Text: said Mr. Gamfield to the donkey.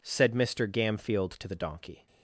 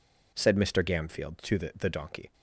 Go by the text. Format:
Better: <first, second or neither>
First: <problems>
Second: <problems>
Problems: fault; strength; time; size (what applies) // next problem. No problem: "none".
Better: first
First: none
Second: says "the" twice; at 1.7 s